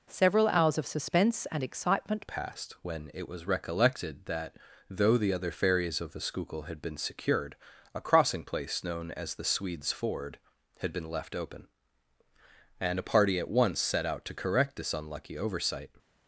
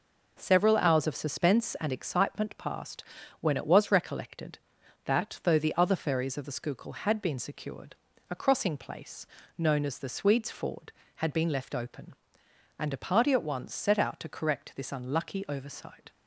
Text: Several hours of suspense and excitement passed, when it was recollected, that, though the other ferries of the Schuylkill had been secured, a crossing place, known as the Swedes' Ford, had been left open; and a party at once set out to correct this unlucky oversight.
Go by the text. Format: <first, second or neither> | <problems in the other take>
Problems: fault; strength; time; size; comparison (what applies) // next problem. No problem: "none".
second | changes voice at "passed"; from 2.2 s on; 13.7 s long